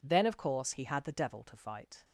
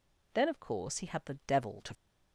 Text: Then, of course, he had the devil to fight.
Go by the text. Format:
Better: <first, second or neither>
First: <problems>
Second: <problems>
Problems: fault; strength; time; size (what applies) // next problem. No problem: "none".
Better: first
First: none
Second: stops before "fight"; at 1.9 s